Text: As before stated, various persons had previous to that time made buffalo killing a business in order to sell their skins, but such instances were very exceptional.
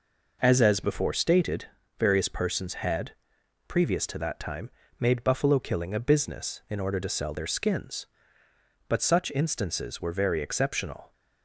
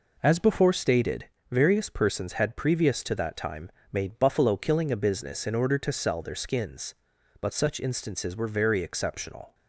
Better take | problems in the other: second | says "As" twice; at 0.6 s // pauses between "had" and "previous"; noticeable; at 3.1 s; 0.56 s long // pauses between "time" and "made"; slight; at 4.6 s; 0.28 s long; slight in the second

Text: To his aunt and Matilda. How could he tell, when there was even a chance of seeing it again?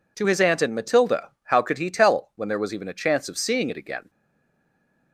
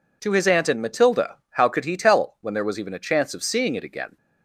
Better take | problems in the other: second | stays silent after the last word; from 4.0 s on; 1.1 s long

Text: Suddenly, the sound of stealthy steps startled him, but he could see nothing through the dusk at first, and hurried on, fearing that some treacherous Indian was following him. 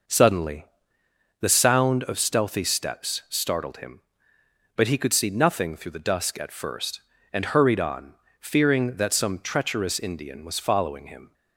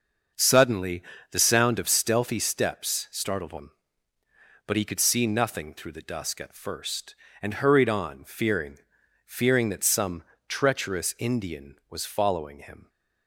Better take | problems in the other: first | starts louder than the rest; until 1.6 s; 6.5 dB // says "fearing" twice; at 9.2 s // pauses between "some" and "treacherous"; slight; at 10.2 s; 0.26 s long

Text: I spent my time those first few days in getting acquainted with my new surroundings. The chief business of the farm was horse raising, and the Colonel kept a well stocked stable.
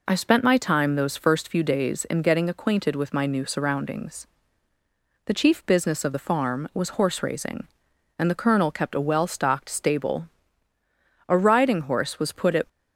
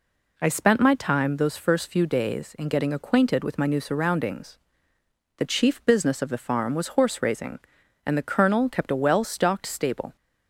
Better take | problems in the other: second | goes on to say "A riding horse was put at"; from 11.2 s on; 1.3 s long

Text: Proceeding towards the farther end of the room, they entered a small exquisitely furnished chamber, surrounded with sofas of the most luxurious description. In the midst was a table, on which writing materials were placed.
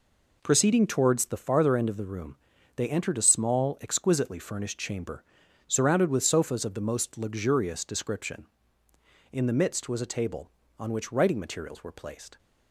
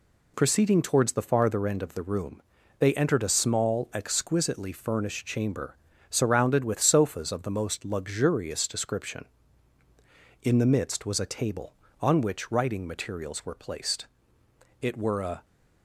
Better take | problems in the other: first | goes on to say "It were a"; noticeable; from 14.8 s on; 0.64 s long

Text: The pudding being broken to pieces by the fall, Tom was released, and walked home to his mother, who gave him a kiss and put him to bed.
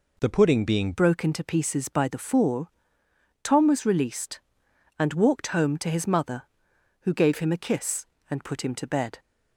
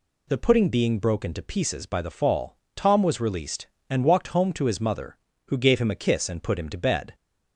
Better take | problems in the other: second | changes voice at "broken"; from 0.9 s on; 8.2 s long

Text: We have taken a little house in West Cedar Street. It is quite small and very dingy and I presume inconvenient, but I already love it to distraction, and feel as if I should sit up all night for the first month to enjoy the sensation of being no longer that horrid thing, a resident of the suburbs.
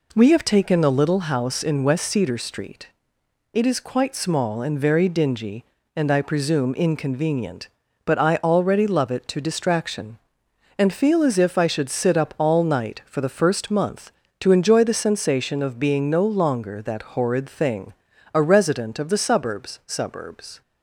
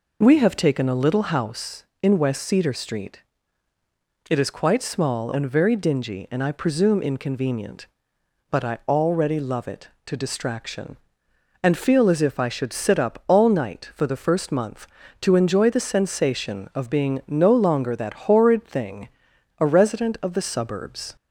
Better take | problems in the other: second | says "suburbs" twice; at 19.8 s

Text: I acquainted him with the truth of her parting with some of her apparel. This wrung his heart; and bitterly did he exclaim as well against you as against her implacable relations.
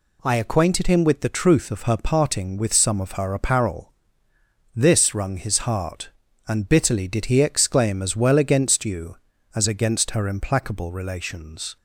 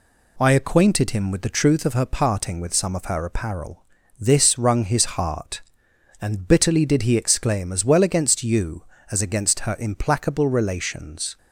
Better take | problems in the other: neither | none

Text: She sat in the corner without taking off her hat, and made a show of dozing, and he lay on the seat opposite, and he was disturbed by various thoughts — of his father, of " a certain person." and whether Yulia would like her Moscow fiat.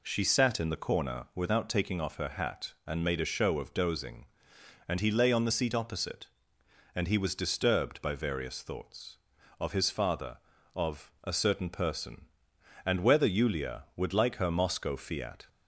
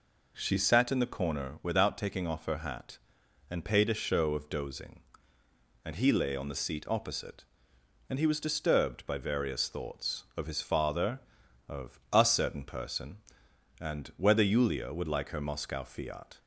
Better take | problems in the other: first | says "paid" for "made"; at 3.6 s

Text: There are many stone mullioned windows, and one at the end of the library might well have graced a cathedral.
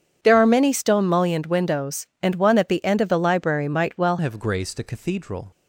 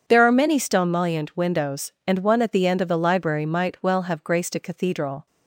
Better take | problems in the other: second | starts louder than the rest; strong; until 1.2 s; 8 dB // changes voice at "have"; from 4.1 s on; 1.3 s long

